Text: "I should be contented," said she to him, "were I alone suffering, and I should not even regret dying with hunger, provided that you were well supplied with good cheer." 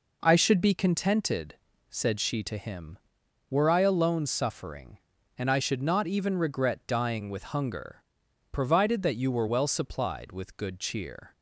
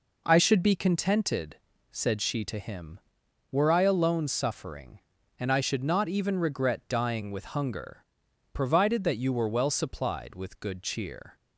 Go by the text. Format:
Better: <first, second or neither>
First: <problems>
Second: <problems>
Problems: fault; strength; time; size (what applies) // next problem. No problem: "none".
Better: neither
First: none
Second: none